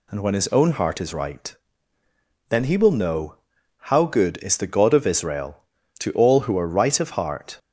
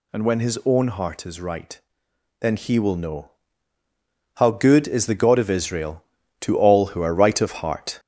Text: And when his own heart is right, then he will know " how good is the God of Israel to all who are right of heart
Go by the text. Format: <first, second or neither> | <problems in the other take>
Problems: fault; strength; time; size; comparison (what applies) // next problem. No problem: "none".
first | gets louder; noticeable; throughout; 4 dB